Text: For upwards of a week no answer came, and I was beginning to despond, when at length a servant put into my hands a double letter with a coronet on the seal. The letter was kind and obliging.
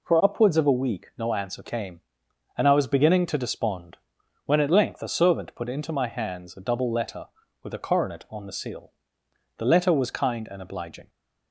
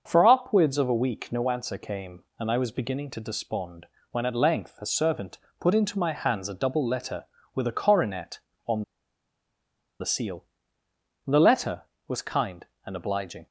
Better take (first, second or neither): first